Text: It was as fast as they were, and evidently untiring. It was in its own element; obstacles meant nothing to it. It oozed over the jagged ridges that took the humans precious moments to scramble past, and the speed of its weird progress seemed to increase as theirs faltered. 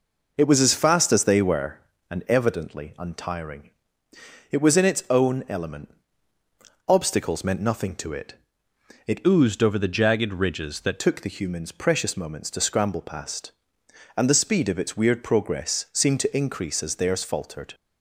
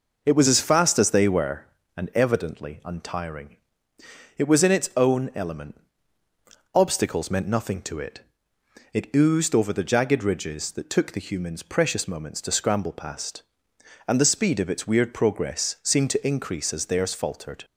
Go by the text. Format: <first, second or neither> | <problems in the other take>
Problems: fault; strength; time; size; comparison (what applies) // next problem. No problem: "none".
second | changes voice from "oozed" to "that"; from 9.2 to 11.0 s; 1.8 s long